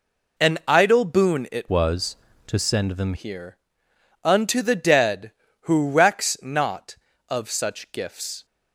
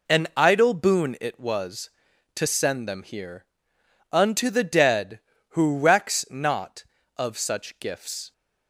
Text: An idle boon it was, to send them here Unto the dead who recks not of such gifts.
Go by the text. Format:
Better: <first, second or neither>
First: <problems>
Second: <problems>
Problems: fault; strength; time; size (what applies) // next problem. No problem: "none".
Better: second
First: changes voice from "was" to "them"; from 1.7 to 3.1 s; 1.4 s long // pauses between "here" and "Unto"; noticeable; at 3.5 s; 0.66 s long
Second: pauses between "here" and "Unto"; noticeable; at 3.4 s; 0.66 s long